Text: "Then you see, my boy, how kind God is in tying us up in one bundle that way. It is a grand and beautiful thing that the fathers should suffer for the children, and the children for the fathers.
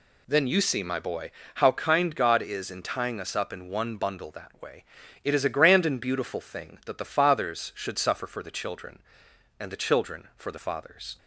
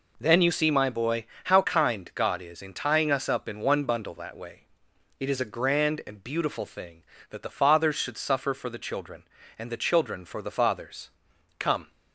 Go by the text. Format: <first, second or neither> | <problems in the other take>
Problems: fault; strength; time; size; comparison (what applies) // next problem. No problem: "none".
first | goes on to say "Come"; slight; from 11.5 s on; 0.32 s long